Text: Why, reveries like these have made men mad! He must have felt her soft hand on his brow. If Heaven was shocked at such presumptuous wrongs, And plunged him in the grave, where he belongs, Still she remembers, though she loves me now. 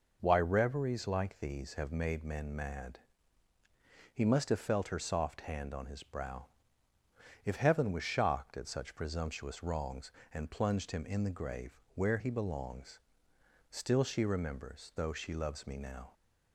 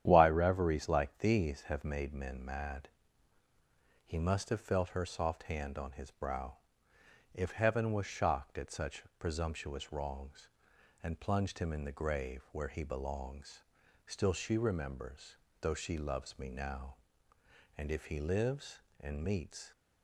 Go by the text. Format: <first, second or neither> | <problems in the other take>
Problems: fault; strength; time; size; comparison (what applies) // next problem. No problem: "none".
first | starts louder than the rest; strong; until 1.0 s; 10 dB // pauses between "such" and "presumptuous"; slight; at 9.0 s; 0.16 s long // goes on to say "And if he lives and meets"; strong; from 17.7 s on; 1.9 s long